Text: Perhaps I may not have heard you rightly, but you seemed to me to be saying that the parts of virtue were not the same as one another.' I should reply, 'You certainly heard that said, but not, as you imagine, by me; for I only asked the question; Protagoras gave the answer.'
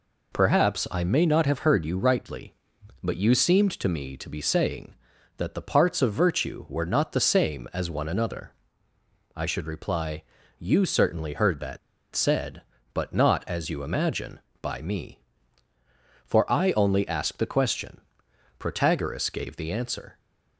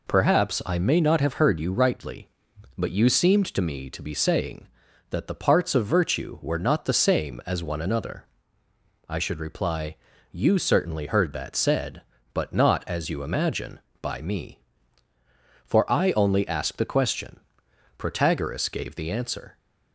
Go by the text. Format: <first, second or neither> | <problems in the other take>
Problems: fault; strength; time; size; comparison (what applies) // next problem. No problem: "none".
second | pauses between "that" and "said"; slight; at 11.7 s; 0.35 s long